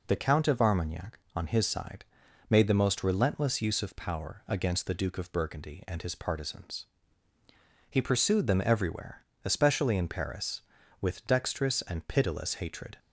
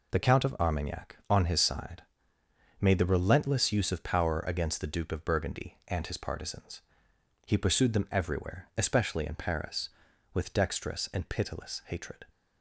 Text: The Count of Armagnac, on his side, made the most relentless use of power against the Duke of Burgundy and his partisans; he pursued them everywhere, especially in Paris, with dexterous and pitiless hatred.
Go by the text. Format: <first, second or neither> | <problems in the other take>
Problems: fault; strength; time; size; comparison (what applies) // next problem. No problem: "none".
first | skips "most"; at 3.0 s